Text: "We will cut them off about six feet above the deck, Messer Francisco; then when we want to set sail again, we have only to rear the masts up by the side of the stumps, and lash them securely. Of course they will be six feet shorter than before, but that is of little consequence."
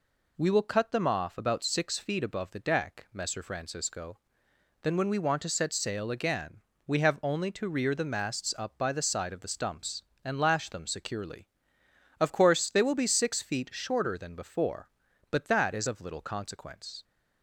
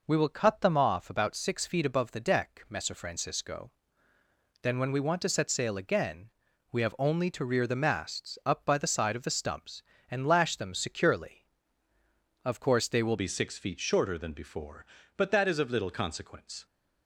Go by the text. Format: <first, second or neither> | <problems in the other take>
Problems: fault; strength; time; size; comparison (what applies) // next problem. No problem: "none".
first | changes voice at "be"; from 13.1 s on; 3.5 s long